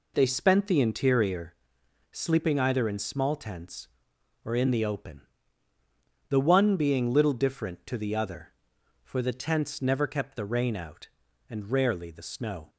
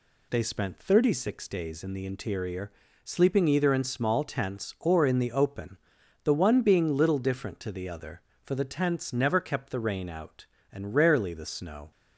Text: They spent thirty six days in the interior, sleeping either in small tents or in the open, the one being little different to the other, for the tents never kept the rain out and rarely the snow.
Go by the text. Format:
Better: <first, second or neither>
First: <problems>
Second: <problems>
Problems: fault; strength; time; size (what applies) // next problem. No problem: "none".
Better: second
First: skips "thirty six days in"; at 0.6 s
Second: none